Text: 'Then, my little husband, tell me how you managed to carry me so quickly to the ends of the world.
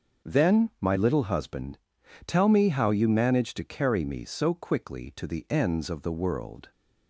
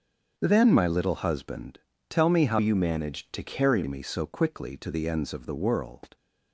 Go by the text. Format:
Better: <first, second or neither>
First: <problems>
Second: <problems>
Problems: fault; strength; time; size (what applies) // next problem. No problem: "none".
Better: first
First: starts louder than the rest; until 1.3 s; 6.5 dB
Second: starts louder than the rest; until 1.3 s; 7 dB // changes voice from "you" to "carry"; from 2.5 to 3.8 s; 1.3 s long